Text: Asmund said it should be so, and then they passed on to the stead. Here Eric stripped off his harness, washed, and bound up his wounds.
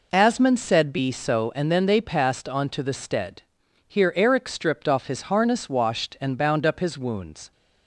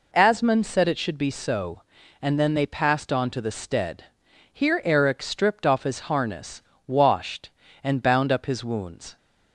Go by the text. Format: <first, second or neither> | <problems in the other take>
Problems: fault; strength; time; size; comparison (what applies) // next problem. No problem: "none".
second | skips "it should"; at 0.9 s